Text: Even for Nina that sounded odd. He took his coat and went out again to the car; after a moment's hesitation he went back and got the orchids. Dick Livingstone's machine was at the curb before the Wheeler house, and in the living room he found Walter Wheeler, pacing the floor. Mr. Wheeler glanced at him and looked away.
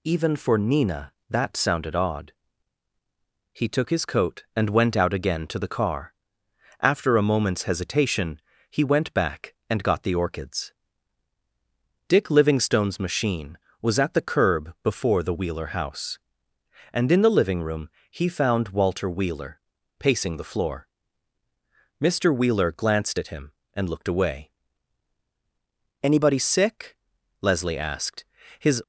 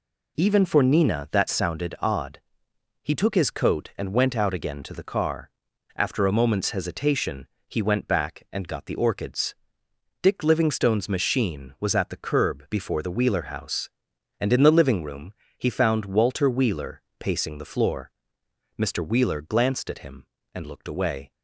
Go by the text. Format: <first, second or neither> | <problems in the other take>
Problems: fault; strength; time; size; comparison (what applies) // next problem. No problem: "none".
second | pauses between "hesitation" and "he"; slight; at 8.3 s; 0.30 s long; slight in the second // pauses between "room" and "he"; slight; at 17.8 s; 0.20 s long; slight in the second // goes on to say "Anybody sick Leslie asked his"; strong; from 26.0 s on; 2.7 s long